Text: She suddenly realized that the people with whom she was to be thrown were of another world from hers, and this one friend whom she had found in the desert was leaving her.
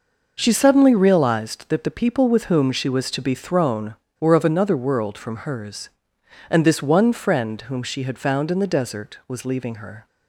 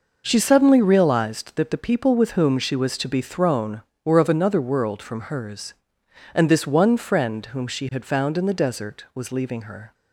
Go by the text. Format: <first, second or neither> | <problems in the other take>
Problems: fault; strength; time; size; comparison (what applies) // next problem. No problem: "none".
neither | none